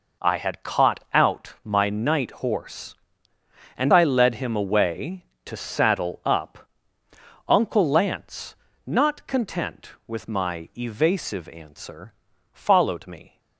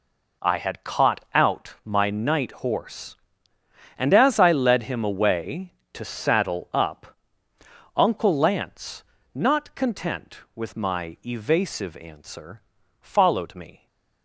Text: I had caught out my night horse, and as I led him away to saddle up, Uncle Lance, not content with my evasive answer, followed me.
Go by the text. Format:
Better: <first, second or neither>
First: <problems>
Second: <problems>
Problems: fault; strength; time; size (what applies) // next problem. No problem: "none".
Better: second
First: skips "as"; at 3.9 s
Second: none